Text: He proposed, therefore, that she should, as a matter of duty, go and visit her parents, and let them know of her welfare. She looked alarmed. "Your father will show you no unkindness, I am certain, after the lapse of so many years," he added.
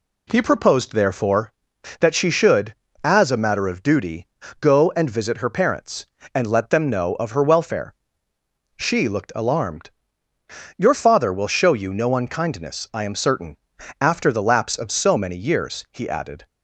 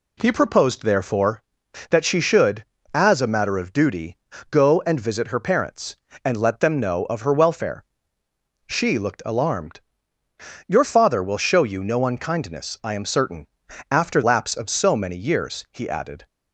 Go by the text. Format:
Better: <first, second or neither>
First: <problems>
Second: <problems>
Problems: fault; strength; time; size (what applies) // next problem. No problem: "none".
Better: first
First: none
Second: skips "the"; at 14.2 s